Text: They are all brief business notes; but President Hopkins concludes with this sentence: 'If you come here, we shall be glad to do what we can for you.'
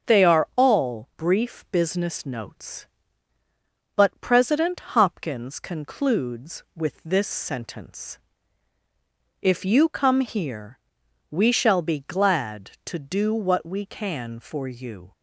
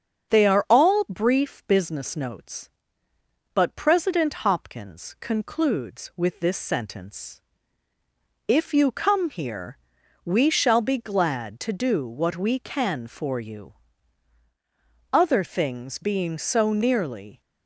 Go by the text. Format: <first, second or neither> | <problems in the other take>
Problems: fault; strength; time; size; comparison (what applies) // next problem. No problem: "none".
first | starts louder than the rest; strong; until 1.3 s; 7 dB; also in the first // goes on to say "Other things being so nearly"; strong; from 15.1 s on; 2.2 s long